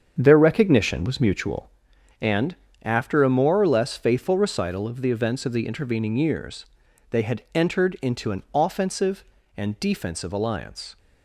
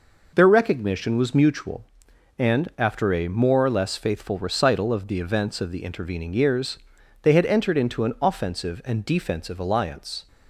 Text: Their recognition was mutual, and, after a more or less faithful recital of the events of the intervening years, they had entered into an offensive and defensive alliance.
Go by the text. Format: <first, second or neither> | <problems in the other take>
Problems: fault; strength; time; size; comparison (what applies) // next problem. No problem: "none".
second | starts louder than the rest; strong; until 1.8 s; 7.5 dB